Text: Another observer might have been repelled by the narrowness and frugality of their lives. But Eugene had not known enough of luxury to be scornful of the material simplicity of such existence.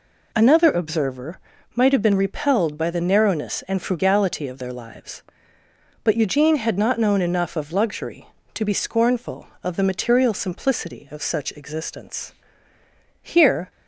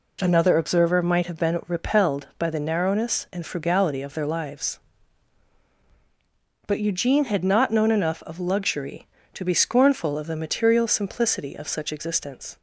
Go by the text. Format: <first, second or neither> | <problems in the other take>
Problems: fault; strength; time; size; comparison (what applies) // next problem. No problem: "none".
second | pauses between "observer" and "might"; slight; at 1.4 s; 0.34 s long // goes on to say "Here"; slight; from 13.2 s on; 0.48 s long